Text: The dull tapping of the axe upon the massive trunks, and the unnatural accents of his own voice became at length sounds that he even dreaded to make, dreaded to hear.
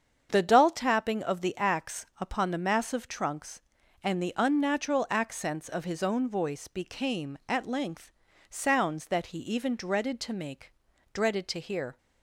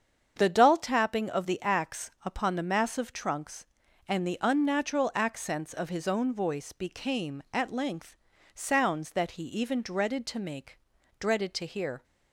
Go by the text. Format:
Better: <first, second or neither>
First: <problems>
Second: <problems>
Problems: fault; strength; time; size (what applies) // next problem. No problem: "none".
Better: neither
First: starts louder than the rest; strong; until 1.3 s; 7.5 dB // pauses between "length" and "sounds"; slight; at 8.1 s; 0.36 s long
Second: starts louder than the rest; strong; until 1.3 s; 7.5 dB // pauses between "length" and "sounds"; slight; at 8.1 s; 0.36 s long